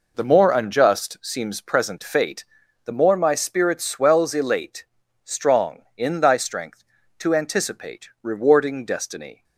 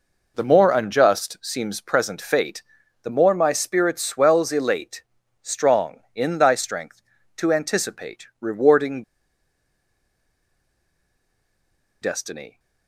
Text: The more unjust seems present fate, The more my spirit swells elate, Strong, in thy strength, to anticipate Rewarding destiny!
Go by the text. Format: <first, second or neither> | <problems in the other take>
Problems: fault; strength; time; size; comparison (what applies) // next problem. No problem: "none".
first | pauses between "Rewarding" and "destiny"; strong; at 9.0 s; 3.0 s long